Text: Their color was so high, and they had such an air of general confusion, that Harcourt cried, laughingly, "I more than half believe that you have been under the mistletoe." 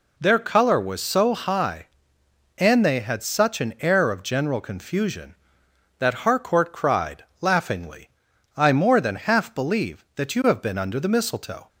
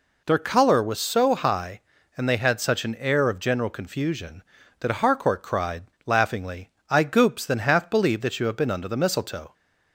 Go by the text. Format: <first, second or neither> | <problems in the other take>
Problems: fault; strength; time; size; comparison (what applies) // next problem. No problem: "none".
first | says "goops" for "more"; at 7.0 s